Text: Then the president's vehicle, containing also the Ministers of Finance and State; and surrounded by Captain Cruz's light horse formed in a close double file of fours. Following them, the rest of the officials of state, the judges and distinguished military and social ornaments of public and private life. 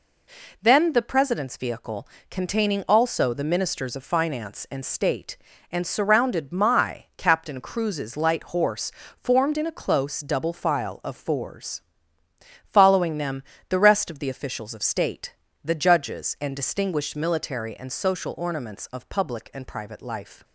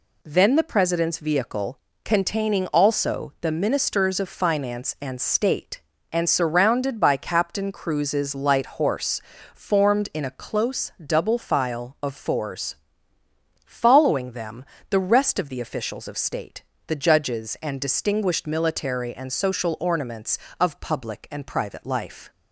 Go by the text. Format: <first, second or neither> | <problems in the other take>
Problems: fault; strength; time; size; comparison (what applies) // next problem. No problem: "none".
second | says "my" for "by"; at 6.5 s // pauses between "horse" and "formed"; slight; at 8.9 s; 0.28 s long; slight in the second